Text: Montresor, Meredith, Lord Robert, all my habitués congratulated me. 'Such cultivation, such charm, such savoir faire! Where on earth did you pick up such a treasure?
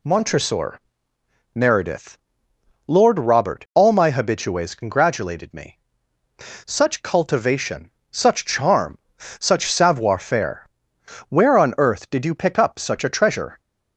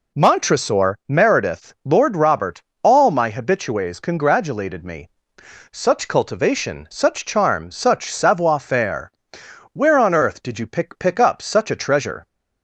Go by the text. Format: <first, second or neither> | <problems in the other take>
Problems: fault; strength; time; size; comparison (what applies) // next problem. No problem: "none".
first | says "pick" twice; at 10.9 s